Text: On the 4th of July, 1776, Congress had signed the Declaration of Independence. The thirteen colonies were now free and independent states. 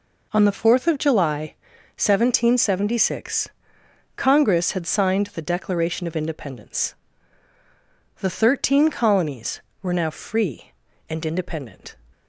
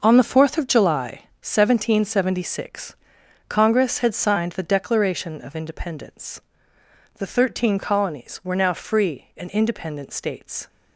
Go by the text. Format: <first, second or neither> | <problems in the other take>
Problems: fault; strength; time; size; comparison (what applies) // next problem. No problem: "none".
second | stops before "states"; at 12.1 s